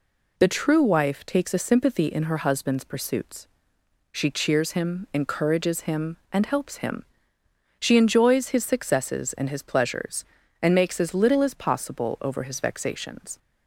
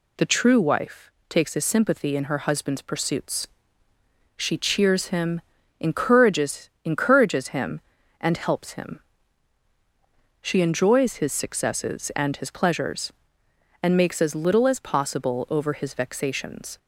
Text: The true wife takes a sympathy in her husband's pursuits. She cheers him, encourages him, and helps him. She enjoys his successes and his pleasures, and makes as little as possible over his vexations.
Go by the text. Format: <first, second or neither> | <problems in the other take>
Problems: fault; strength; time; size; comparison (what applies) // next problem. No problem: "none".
first | pauses between "wife" and "takes"; slight; at 1.0 s; 0.18 s long // says "encourages" twice; at 6.8 s